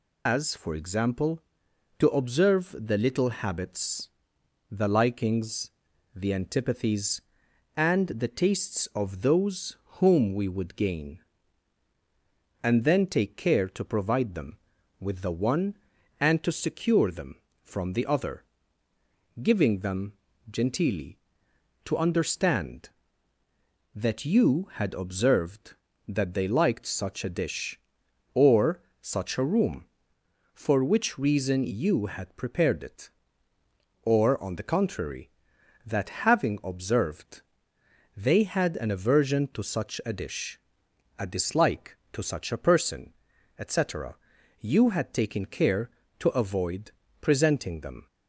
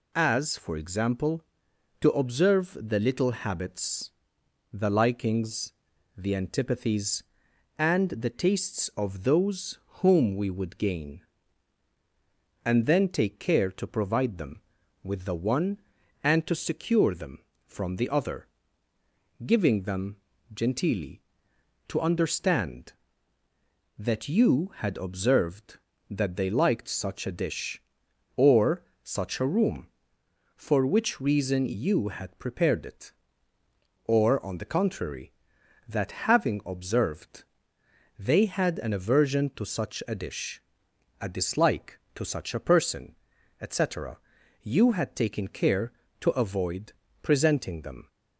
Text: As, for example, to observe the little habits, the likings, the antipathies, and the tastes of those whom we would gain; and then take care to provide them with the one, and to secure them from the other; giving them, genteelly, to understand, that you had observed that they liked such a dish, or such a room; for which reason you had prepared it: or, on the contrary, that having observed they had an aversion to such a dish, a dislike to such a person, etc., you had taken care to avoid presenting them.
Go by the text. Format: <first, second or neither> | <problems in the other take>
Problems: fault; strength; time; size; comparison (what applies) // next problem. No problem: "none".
second | loses the start of "As"; at 0.2 s; 125 ms // pauses between "those" and "whom"; slight; at 9.7 s; 0.24 s long; slight in the second // pauses between "or" and "such"; slight; at 28.8 s; 0.20 s long; slight in the second // pauses between "that" and "having"; slight; at 36.0 s; 0.16 s long; slight in the second // pauses between "observed" and "they"; noticeable; at 37.4 s; 0.76 s long; noticeable in the second // pauses between "avoid" and "presenting"; slight; at 46.9 s; 0.30 s long; slight in the second